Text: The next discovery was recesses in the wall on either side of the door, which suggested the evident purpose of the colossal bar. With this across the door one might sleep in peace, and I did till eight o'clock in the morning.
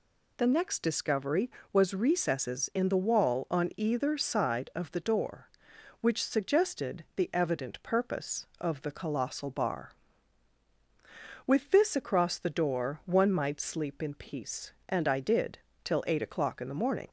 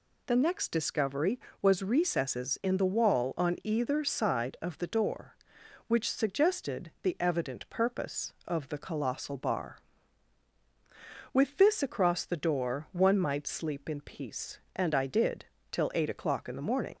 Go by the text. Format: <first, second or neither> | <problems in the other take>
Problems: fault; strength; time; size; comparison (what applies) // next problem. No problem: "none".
neither | pauses between "did" and "till"; slight; the same in both